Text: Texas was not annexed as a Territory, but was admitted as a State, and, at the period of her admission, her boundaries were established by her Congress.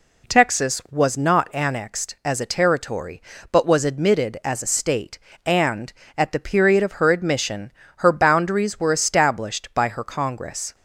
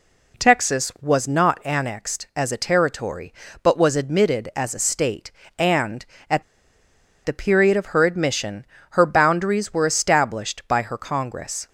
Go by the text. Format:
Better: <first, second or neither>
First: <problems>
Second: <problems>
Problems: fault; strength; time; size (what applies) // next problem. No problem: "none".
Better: first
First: none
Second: pauses between "at" and "the"; noticeable; at 6.4 s; 0.82 s long